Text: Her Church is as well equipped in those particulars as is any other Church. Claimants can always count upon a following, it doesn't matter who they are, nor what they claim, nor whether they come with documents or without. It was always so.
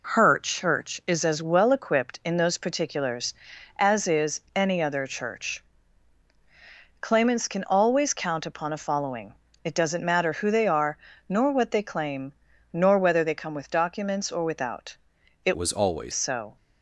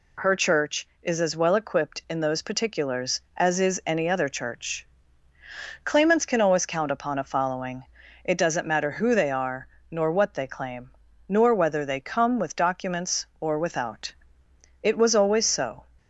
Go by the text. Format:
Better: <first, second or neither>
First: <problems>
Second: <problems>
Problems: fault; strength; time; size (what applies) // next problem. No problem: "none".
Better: second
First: pauses between "is" and "any"; slight; at 4.3 s; 0.16 s long // changes voice from "was" to "always"; from 15.5 to 16.1 s; 0.6 s long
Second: none